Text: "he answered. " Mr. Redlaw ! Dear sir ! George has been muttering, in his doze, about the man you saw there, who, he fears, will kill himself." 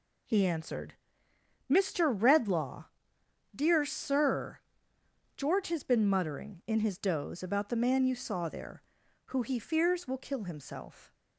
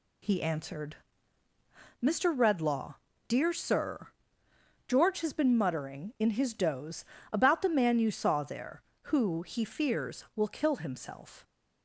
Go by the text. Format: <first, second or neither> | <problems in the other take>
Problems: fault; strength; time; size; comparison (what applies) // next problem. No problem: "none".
neither | none